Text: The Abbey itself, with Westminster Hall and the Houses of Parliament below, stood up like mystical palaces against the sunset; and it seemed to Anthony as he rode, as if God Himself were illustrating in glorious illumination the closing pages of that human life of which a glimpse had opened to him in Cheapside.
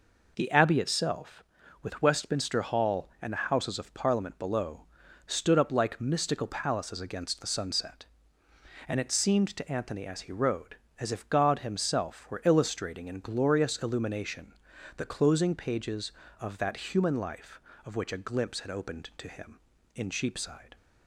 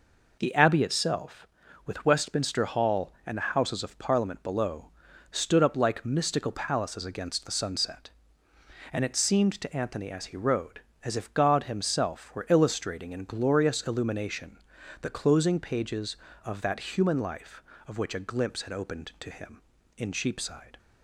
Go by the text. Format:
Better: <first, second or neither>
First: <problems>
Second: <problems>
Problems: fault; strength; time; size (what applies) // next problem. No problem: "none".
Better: neither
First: pauses between "illumination" and "the"; at 14.5 s; 0.44 s long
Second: pauses between "illumination" and "the"; at 14.5 s; 0.44 s long